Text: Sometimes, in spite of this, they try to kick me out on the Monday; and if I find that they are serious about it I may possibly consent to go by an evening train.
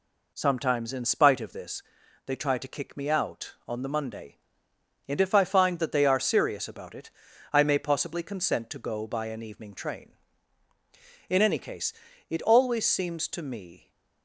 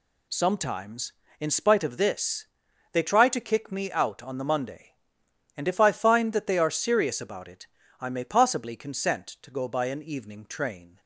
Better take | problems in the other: second | pauses between "it" and "I"; at 7.0 s; 0.42 s long; slight in the second // goes on to say "In any case it always seems to me"; strong; from 11.2 s on; 2.6 s long

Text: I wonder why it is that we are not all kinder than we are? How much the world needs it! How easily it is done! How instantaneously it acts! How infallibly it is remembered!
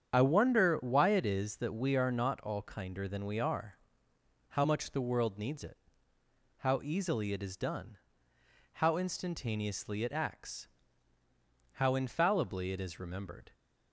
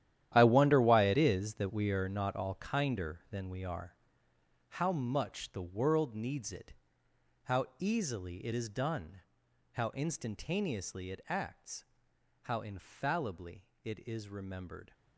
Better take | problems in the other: first | gets quieter; strong; throughout; 14 dB // starts louder than the rest; strong; until 1.3 s; 11.5 dB; strong in the first // pauses between "infallibly" and "it"; slight; at 13.6 s; 0.18 s long

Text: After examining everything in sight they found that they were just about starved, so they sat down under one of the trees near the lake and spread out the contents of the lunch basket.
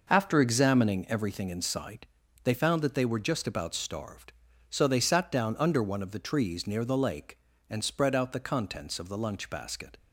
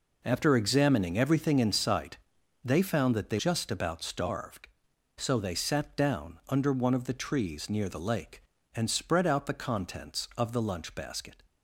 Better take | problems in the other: first | pauses between "sight" and "they"; noticeable; at 2.1 s; 0.48 s long; also in the first // skips "were"; at 3.3 s

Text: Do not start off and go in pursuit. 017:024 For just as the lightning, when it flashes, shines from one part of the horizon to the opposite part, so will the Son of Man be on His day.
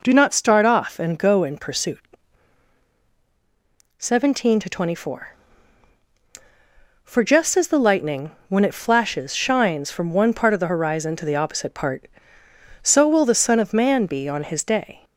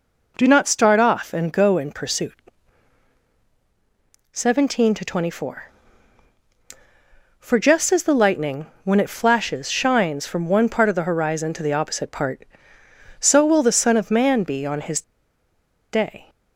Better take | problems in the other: first | pauses between "His" and "day"; noticeable; at 15.0 s; 0.91 s long

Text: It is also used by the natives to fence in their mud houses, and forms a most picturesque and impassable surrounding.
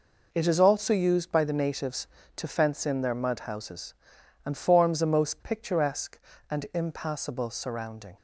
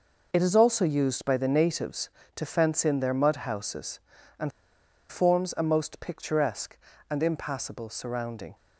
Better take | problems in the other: first | pauses between "and" and "forms"; noticeable; at 4.5 s; 0.59 s long

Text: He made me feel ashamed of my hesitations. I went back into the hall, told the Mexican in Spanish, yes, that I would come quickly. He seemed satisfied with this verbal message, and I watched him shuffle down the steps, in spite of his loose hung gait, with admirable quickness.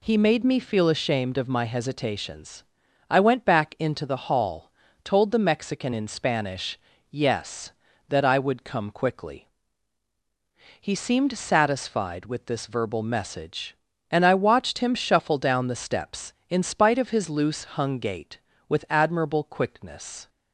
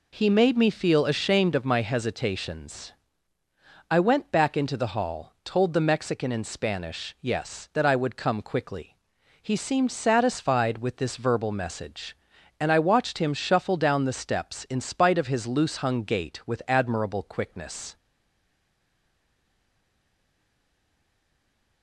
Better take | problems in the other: first | stays silent after the last word; strong; from 17.9 s on; 3.9 s long

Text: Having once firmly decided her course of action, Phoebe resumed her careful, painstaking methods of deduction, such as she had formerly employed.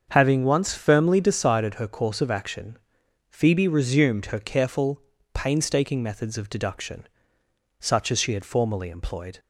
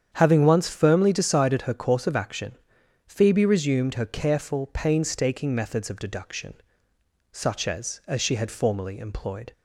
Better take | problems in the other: first | starts louder than the rest; strong; until 1.1 s; 8.5 dB; also in the first // says "as" twice; at 8.0 s

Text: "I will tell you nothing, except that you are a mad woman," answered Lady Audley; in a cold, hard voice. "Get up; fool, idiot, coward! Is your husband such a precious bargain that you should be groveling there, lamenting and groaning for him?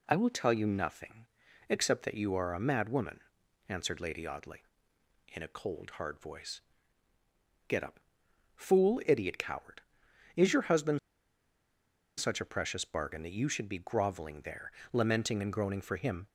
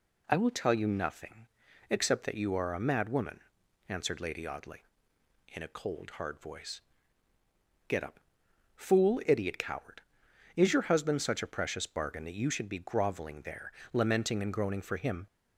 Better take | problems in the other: second | pauses between "husband" and "such"; at 10.9 s; 1.1 s long

